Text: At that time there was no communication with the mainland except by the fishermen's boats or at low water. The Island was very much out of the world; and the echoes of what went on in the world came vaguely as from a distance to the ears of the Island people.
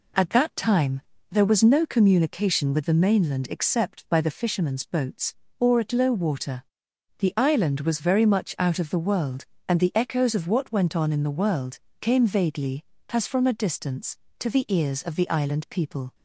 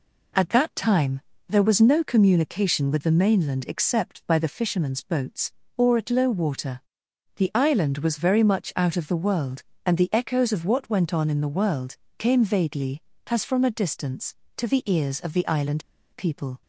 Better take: first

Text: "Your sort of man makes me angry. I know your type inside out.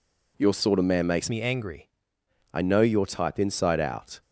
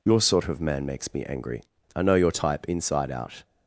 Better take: second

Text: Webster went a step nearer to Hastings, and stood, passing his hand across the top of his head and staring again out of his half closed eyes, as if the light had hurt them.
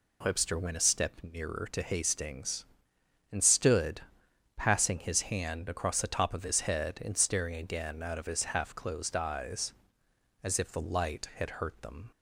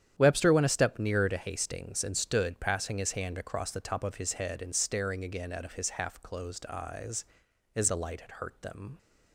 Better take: first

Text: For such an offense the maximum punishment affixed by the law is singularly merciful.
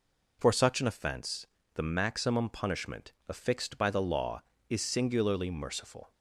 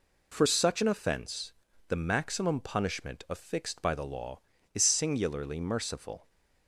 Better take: second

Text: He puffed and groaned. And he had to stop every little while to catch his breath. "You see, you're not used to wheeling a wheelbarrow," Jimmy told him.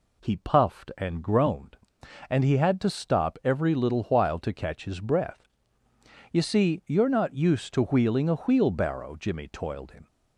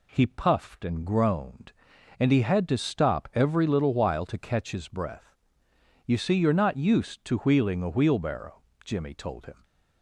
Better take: second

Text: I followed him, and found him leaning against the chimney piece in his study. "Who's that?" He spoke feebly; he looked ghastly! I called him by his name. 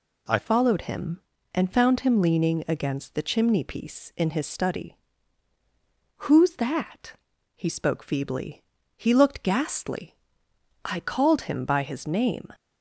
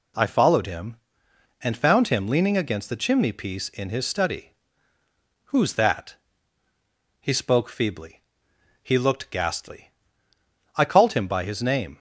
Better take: second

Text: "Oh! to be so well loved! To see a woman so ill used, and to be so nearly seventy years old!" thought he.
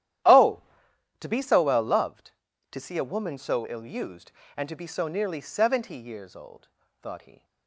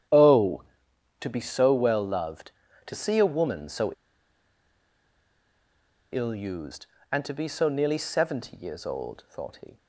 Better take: first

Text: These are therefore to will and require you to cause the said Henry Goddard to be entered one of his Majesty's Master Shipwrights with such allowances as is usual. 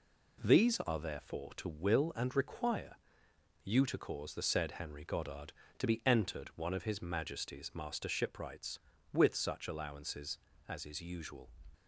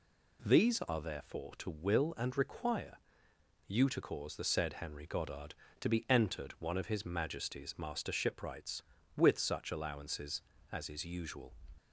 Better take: second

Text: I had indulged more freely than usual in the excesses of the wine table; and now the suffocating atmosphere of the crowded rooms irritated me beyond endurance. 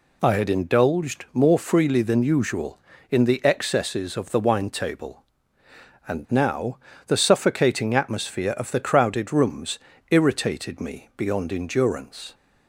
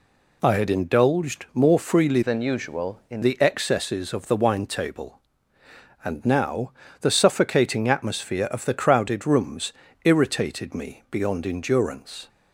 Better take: first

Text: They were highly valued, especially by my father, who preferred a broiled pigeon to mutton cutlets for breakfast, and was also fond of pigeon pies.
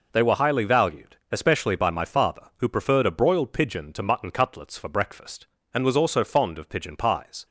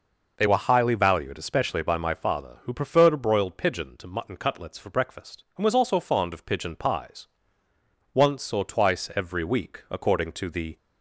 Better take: first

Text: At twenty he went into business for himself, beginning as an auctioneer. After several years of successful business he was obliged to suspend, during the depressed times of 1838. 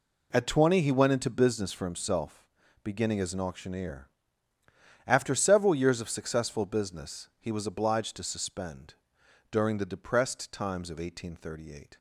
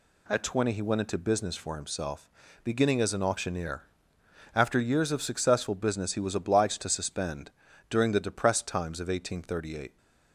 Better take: first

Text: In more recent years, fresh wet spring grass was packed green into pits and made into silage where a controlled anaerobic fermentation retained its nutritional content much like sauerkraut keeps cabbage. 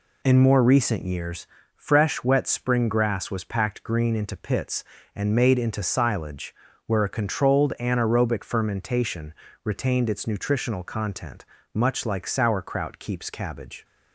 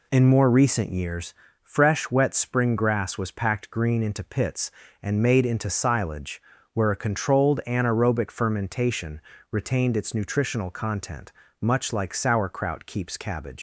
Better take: first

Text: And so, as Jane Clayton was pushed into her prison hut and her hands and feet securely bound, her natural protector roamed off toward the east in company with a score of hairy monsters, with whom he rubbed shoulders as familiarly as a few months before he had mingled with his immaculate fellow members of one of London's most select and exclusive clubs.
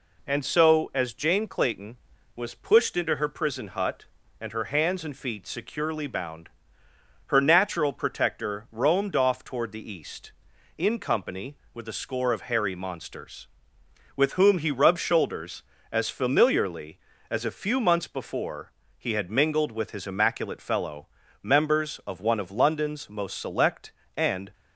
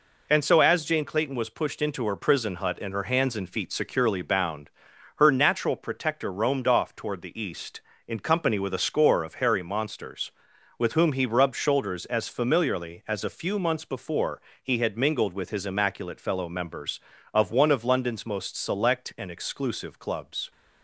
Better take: second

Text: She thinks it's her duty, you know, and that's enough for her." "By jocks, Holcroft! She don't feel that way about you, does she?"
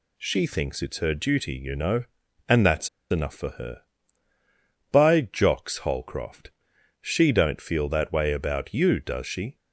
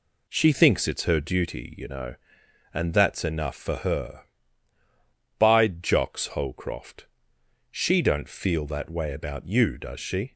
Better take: second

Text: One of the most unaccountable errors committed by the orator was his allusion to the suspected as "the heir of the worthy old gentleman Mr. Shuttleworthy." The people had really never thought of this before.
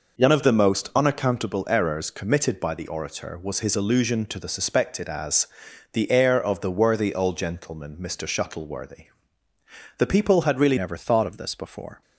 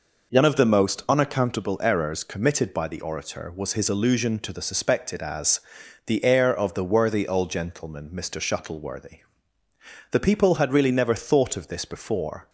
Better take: second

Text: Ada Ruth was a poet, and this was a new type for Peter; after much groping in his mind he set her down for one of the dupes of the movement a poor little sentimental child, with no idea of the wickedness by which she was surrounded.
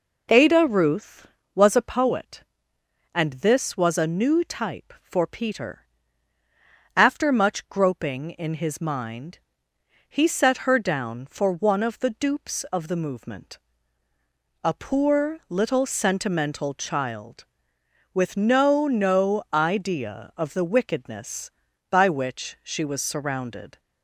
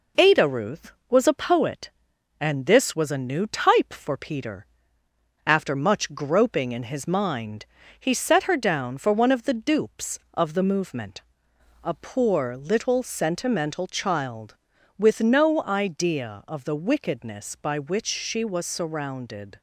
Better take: second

